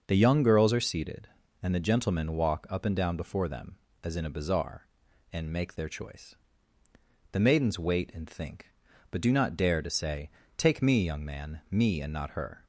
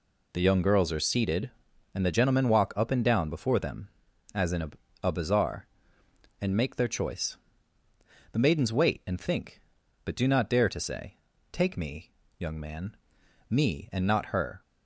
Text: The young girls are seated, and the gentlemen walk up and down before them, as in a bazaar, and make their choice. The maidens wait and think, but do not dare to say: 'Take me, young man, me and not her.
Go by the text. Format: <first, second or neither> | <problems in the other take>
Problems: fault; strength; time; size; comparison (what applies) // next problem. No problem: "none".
first | says "a" twice; at 5.0 s